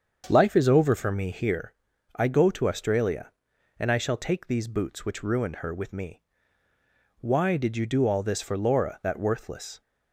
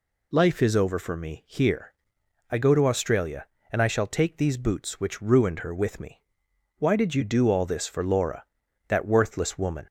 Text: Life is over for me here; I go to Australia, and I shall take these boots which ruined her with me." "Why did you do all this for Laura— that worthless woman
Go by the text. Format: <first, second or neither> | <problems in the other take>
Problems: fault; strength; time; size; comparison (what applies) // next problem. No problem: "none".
second | starts louder than the rest; strong; until 1.3 s; 7 dB // stops before "woman"; at 9.8 s